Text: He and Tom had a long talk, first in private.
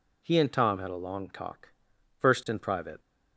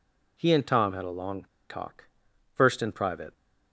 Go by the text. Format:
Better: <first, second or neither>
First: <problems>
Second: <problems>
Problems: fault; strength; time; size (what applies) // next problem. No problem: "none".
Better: first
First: none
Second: pauses between "long" and "talk"; slight; at 1.4 s; 0.24 s long